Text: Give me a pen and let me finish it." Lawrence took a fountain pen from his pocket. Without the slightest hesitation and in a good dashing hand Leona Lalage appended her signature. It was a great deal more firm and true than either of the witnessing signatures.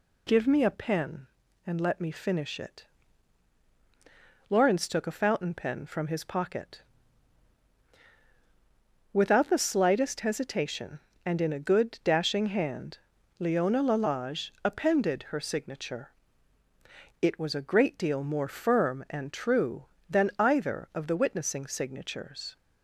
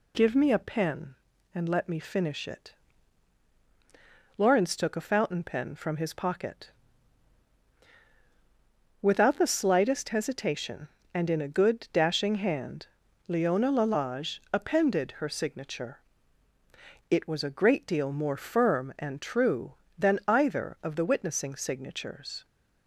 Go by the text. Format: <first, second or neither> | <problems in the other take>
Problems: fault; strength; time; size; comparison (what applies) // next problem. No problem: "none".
neither | pauses between "hand" and "Leona"; the same in both